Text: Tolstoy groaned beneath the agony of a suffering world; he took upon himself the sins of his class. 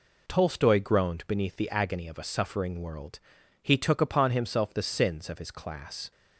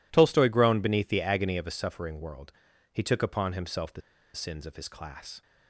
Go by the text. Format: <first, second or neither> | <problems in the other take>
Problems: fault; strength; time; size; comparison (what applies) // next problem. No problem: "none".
first | pauses between "the" and "sins"; slight; at 4.0 s; 0.33 s long